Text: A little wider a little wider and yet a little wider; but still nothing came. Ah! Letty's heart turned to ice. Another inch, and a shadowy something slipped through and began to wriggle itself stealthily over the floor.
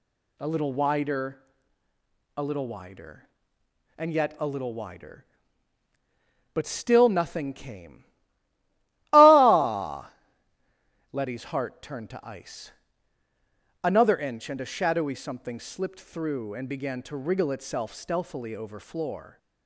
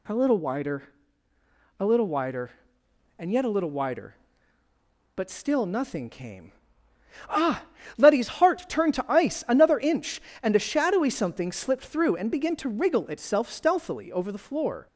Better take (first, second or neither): second